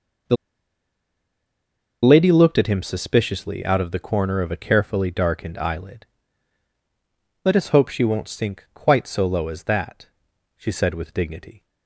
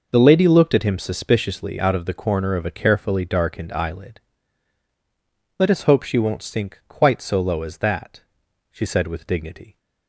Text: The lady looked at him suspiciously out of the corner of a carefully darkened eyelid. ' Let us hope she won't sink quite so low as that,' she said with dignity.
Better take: second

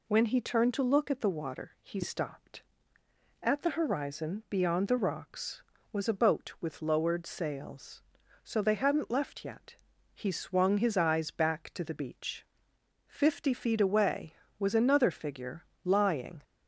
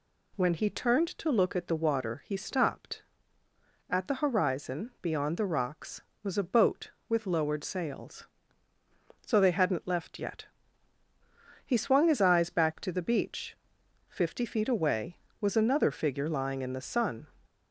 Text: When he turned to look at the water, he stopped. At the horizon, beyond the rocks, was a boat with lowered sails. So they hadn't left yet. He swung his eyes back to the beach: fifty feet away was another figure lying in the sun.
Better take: second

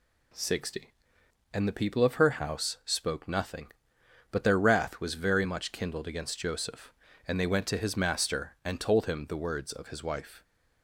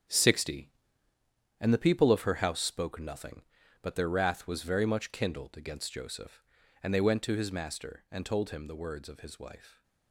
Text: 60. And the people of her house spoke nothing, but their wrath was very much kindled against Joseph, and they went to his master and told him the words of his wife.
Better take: first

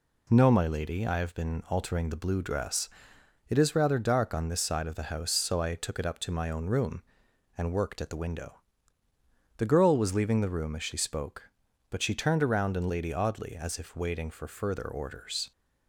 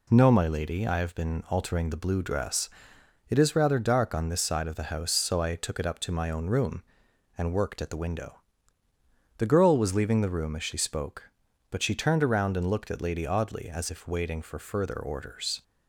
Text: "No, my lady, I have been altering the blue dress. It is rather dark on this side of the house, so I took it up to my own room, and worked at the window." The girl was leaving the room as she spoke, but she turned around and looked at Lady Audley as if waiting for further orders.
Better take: second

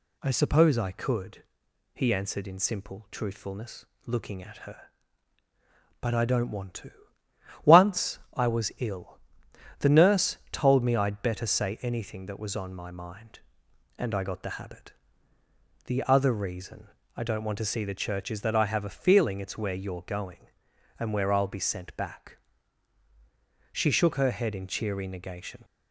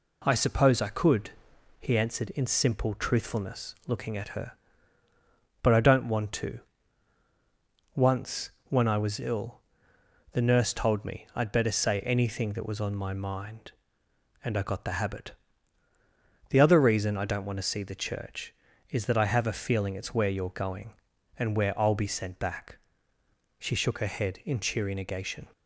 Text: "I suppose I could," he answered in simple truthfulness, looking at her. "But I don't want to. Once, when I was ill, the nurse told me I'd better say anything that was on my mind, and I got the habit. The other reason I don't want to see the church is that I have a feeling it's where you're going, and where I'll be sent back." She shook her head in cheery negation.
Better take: second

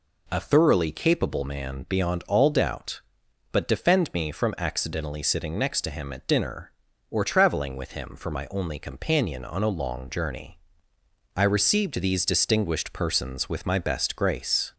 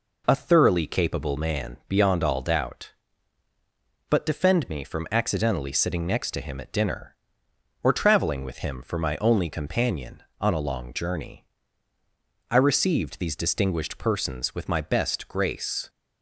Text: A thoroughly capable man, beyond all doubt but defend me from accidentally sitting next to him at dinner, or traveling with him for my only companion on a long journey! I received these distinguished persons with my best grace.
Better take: neither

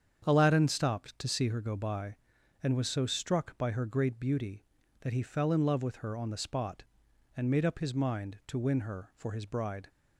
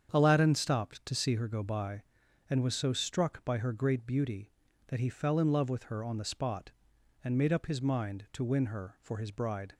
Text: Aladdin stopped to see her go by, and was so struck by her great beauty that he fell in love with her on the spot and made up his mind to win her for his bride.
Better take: neither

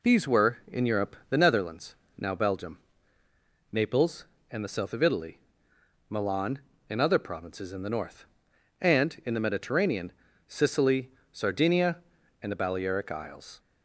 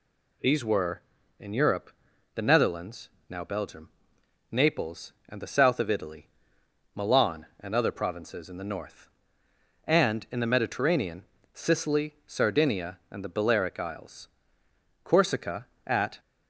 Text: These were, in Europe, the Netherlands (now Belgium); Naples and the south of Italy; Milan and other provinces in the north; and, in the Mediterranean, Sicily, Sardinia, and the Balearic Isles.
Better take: first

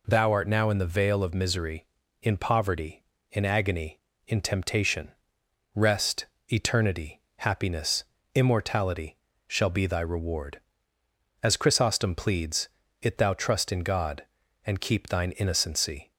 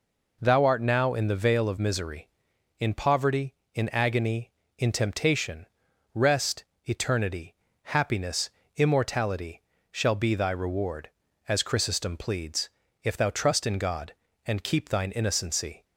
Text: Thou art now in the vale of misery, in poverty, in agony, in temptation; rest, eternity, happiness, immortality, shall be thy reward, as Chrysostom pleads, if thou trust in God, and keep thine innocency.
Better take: second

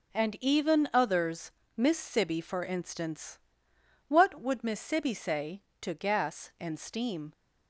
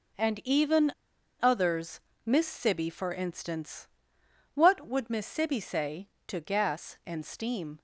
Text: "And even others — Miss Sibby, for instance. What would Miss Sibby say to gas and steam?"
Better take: first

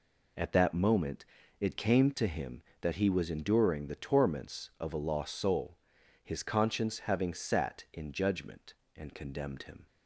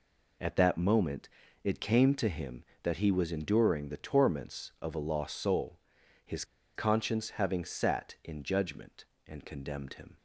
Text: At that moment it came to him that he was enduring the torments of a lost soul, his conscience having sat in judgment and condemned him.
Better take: first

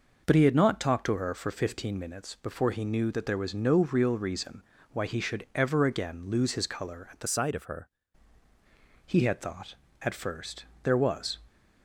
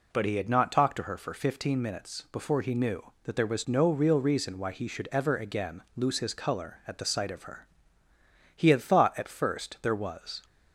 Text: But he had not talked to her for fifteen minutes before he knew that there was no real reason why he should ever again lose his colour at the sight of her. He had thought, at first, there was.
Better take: second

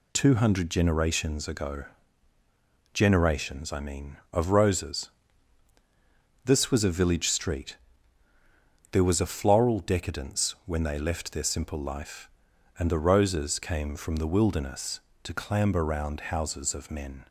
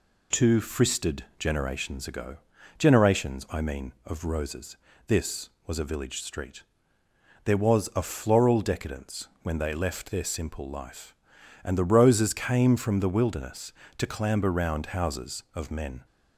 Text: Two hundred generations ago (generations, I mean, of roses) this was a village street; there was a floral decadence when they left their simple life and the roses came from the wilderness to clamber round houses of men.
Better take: first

